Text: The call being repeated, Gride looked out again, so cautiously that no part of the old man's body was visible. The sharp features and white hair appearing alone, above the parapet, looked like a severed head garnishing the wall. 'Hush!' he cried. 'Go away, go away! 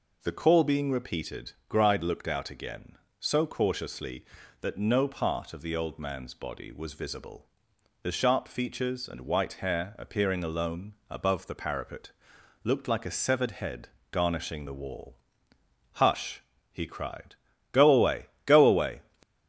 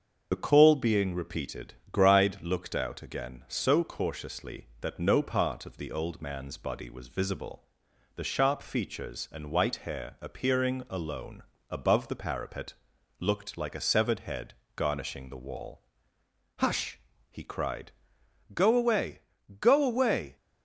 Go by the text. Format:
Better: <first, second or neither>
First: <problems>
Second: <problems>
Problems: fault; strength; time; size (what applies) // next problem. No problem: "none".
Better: first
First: pauses between "head" and "garnishing"; slight; at 13.8 s; 0.22 s long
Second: loses the start of "The"; at 0.3 s; 35 ms // starts louder than the rest; until 1.3 s; 7 dB // pauses between "head" and "garnishing"; slight; at 14.5 s; 0.22 s long